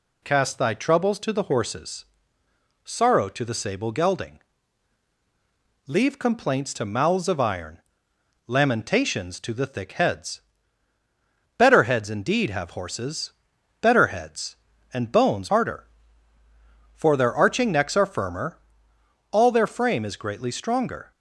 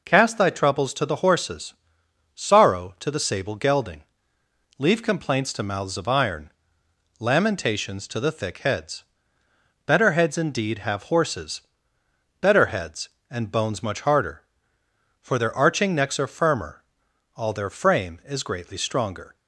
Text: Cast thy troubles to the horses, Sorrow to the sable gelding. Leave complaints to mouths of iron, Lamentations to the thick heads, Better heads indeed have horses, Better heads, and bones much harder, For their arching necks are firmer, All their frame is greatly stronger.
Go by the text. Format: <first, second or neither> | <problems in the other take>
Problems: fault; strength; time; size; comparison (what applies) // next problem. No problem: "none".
second | skips "much"; at 15.4 s